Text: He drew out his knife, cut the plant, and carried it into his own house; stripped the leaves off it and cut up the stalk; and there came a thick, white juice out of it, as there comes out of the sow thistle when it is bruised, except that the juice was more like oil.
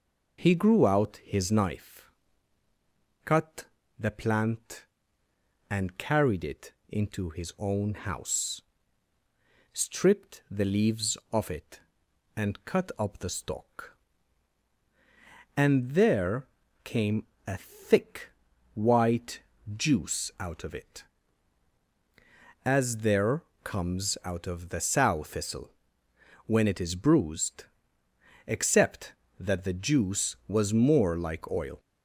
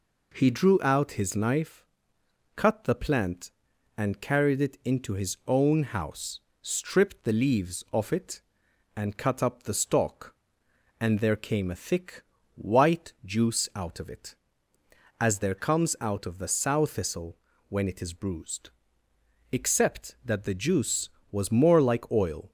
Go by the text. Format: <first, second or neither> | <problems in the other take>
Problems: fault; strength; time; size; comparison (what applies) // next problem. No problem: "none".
second | says "grew" for "drew"; at 0.5 s // pauses between "cut" and "the"; slight; at 3.6 s; 0.34 s long // pauses between "it" and "into"; slight; at 6.7 s; 0.16 s long // pauses between "there" and "came"; at 16.4 s; 0.38 s long // pauses between "came" and "a"; slight; at 17.2 s; 0.20 s long // pauses between "white" and "juice"; slight; at 19.4 s; 0.34 s long // pauses between "there" and "comes"; slight; at 23.4 s; 0.22 s long // pauses between "thistle" and "when"; noticeable; at 25.7 s; 0.74 s long; slight in the second